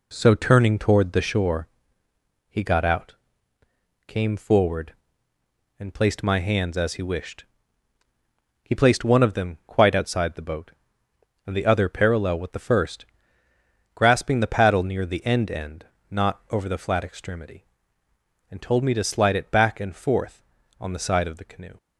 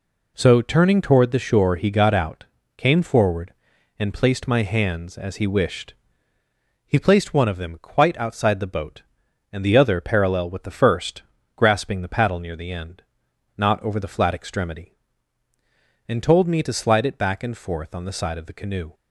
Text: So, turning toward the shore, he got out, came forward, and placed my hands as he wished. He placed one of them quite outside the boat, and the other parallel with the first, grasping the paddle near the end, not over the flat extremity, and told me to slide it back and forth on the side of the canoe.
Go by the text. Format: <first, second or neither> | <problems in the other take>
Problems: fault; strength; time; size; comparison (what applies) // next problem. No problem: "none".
second | says "end" twice; at 15.4 s